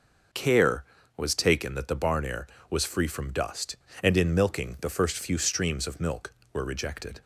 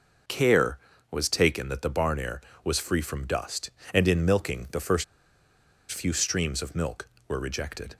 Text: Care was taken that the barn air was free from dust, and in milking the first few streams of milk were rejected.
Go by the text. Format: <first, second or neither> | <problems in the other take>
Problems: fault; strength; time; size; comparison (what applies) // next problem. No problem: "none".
first | pauses between "first" and "few"; noticeable; at 5.0 s; 0.87 s long